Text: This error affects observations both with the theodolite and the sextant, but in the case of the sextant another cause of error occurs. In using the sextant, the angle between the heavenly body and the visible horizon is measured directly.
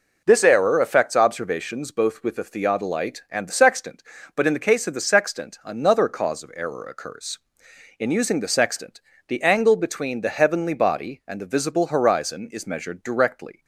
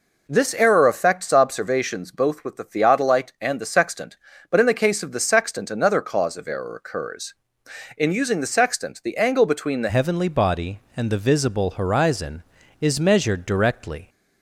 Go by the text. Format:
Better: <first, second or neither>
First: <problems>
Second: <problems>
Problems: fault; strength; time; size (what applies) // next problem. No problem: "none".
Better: first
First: none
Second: changes voice at "heavenly"; from 9.8 s on; 4.2 s long